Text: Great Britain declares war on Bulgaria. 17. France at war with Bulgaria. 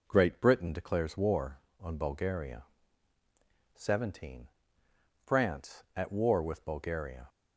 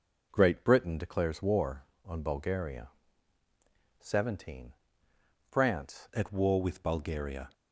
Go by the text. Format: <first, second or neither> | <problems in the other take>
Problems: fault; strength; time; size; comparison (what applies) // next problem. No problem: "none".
first | changes voice at "at"; from 6.1 s on; 1.3 s long